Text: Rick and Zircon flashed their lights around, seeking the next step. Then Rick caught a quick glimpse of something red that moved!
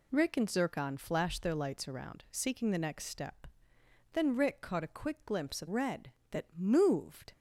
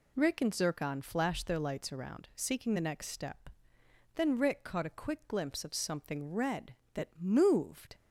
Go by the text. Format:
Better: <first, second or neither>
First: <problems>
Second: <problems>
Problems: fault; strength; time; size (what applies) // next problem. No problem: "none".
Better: second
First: skips "something"; at 5.6 s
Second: none